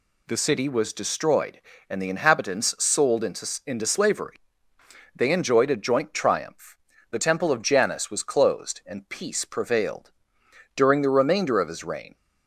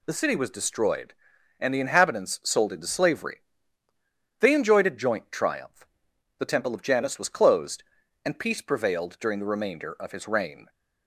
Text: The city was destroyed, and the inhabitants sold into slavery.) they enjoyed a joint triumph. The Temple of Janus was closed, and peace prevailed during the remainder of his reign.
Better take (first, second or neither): second